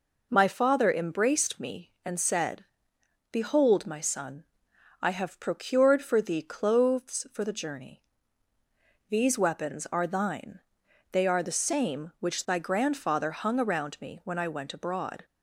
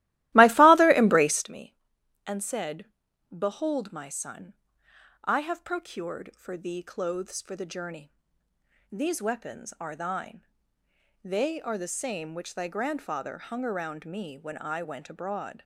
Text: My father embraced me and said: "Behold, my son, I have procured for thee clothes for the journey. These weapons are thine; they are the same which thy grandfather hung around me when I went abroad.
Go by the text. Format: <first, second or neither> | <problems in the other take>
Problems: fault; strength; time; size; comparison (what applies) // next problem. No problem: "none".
first | starts louder than the rest; strong; until 1.5 s; 16.5 dB